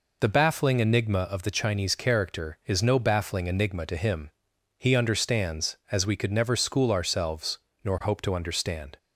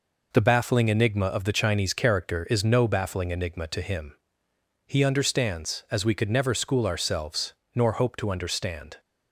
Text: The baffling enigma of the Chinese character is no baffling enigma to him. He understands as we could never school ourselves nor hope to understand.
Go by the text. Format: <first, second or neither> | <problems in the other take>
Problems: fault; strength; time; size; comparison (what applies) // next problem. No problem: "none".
neither | pauses between "ourselves" and "nor"; slight; the same in both